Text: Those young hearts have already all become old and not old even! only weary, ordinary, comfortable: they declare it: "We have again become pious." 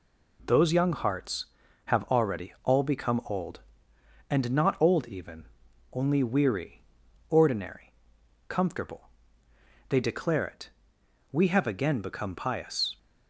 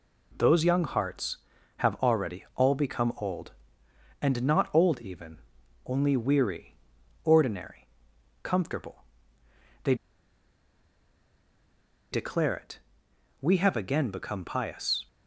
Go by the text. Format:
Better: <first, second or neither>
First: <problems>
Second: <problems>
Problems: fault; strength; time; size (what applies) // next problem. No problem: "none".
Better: first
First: none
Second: pauses between "they" and "declare"; strong; at 9.9 s; 2.1 s long